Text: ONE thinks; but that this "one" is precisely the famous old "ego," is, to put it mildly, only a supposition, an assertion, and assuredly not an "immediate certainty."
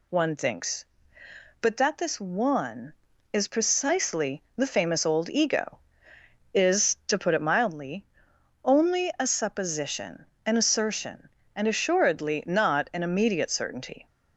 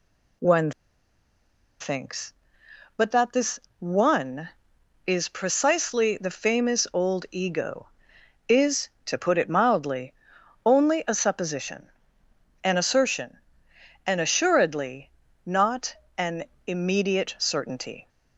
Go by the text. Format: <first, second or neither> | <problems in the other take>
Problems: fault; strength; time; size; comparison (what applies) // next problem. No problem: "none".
first | pauses between "ONE" and "thinks"; at 0.7 s; 1.0 s long // pauses between "this" and "one"; slight; at 3.6 s; 0.18 s long // pauses between "assuredly" and "not"; slight; at 15.0 s; 0.36 s long // pauses between "not" and "an"; slight; at 15.9 s; 0.24 s long // pauses between "an" and "immediate"; slight; at 16.4 s; 0.24 s long